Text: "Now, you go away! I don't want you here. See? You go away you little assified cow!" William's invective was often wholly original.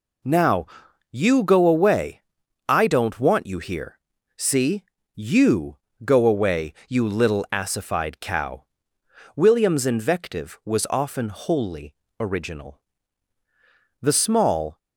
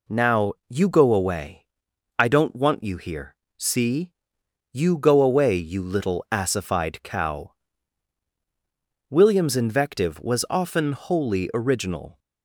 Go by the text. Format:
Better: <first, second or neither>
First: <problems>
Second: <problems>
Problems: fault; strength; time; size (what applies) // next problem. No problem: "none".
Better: second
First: pauses between "You" and "go"; slight; at 5.7 s; 0.26 s long // pauses between "away" and "you"; slight; at 6.7 s; 0.16 s long // pauses between "wholly" and "original"; slight; at 11.9 s; 0.28 s long // goes on to say "The small"; noticeable; from 13.9 s on; 0.78 s long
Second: none